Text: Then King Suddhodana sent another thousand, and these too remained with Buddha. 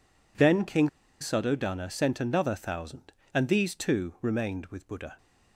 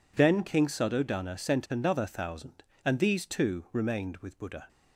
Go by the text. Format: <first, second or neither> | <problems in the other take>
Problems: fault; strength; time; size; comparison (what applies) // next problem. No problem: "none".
second | pauses between "King" and "Suddhodana"; slight; at 0.8 s; 0.31 s long